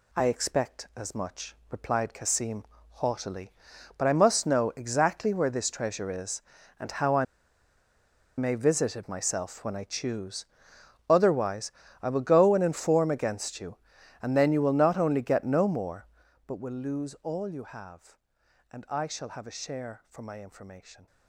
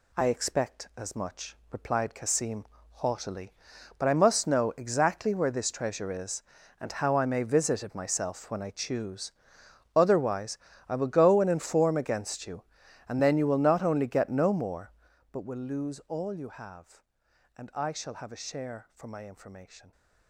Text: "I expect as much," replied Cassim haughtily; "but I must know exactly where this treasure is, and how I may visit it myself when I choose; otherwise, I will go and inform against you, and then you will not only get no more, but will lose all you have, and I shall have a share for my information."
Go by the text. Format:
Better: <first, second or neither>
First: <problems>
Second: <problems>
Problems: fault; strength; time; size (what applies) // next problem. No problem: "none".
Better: second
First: pauses between "Cassim" and "haughtily"; slight; at 2.6 s; 0.24 s long // pauses between "I" and "may"; at 7.2 s; 1.1 s long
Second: pauses between "Cassim" and "haughtily"; slight; at 2.6 s; 0.24 s long